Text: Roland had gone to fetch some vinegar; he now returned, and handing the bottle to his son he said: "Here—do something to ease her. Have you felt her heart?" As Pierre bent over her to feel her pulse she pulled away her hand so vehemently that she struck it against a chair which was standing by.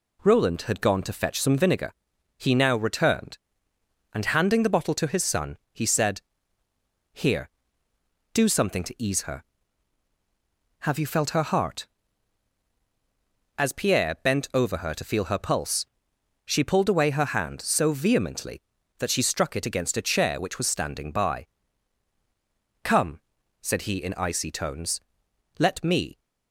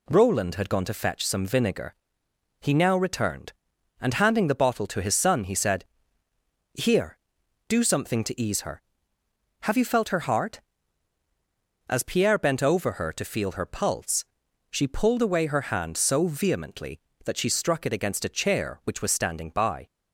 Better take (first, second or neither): second